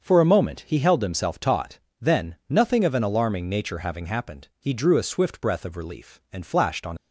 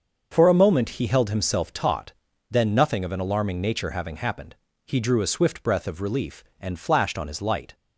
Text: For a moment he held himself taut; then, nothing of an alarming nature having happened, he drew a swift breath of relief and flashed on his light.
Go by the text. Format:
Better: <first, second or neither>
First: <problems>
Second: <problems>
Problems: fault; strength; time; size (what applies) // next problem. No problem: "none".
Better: second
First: starts louder than the rest; until 1.0 s; 6.5 dB // stops before "his light"; at 6.9 s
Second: starts louder than the rest; until 1.3 s; 6.5 dB